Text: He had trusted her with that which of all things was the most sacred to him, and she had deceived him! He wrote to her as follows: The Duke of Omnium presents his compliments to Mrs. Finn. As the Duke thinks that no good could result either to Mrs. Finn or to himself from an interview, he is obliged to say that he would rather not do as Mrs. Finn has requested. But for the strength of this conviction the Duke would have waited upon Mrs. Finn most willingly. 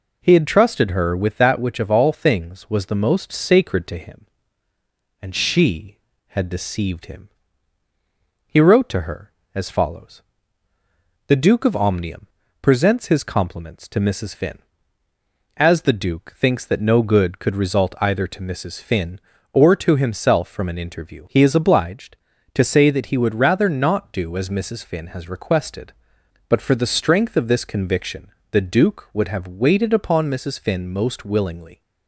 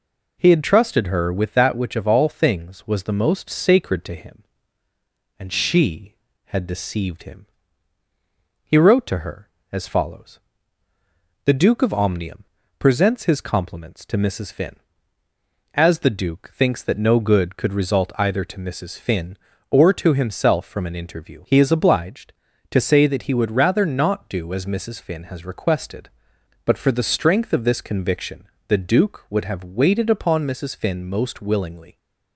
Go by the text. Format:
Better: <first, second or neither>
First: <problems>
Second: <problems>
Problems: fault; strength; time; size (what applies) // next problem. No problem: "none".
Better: neither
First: pauses between "Omnium" and "presents"; slight; at 12.2 s; 0.34 s long // pauses between "conviction" and "the"; slight; at 28.2 s; 0.22 s long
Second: pauses between "Omnium" and "presents"; slight; at 12.4 s; 0.34 s long // pauses between "conviction" and "the"; slight; at 28.4 s; 0.22 s long